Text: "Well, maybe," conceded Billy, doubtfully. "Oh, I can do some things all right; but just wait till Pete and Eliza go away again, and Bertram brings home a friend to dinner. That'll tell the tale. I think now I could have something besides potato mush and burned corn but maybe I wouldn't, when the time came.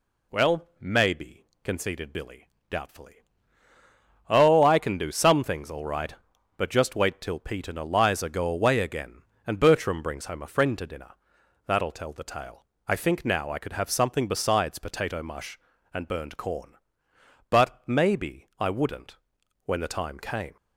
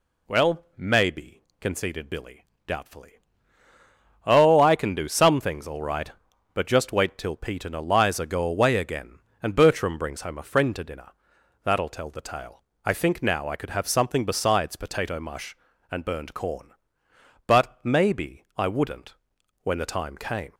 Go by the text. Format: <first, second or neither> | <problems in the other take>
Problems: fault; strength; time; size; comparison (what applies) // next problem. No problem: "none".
neither | none